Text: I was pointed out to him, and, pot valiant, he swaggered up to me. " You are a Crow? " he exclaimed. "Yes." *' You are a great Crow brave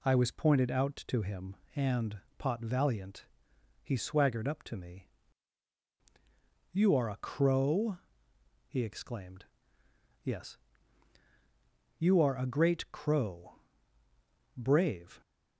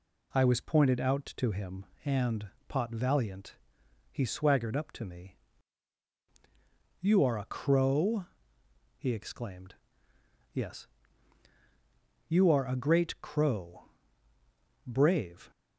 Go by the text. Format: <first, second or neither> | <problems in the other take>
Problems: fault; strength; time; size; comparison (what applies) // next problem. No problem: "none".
neither | pauses between "Crow" and "brave"; the same in both